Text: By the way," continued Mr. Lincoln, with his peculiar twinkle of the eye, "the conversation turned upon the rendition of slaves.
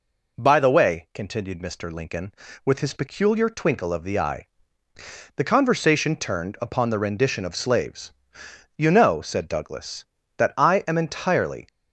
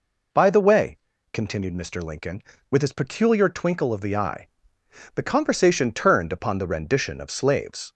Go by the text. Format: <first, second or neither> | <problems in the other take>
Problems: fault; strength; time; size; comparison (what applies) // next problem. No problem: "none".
second | goes on to say "You know said Douglas that I am entirely"; strong; from 8.7 s on; 2.9 s long